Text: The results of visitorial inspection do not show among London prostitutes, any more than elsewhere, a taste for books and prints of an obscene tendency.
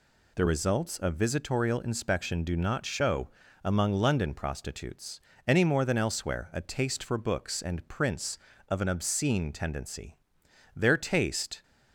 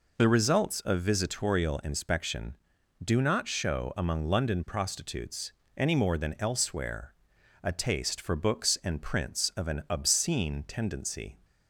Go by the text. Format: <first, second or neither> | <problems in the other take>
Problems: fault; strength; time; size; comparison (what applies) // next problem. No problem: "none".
second | pauses between "show" and "among"; slight; at 3.2 s; 0.36 s long // goes on to say "Their taste"; noticeable; from 10.7 s on; 0.88 s long